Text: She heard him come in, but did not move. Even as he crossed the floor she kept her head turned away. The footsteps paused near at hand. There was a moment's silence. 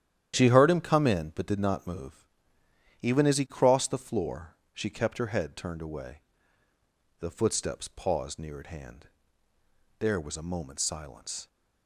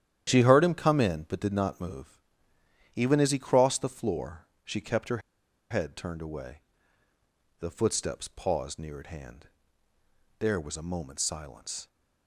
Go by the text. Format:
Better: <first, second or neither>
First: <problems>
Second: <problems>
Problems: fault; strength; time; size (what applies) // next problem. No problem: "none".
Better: first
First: starts louder than the rest; strong; until 1.3 s; 10.5 dB // pauses between "floor" and "she"; slight; at 4.5 s; 0.16 s long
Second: starts louder than the rest; strong; until 1.3 s; 10.5 dB // pauses between "floor" and "she"; slight; at 4.4 s; 0.16 s long // pauses between "her" and "head"; noticeable; at 5.2 s; 0.51 s long